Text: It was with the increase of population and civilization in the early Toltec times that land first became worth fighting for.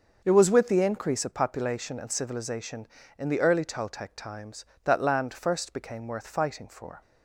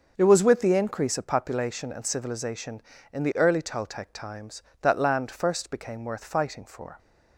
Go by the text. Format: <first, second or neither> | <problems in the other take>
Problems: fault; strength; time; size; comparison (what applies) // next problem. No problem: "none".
neither | starts louder than the rest; the same in both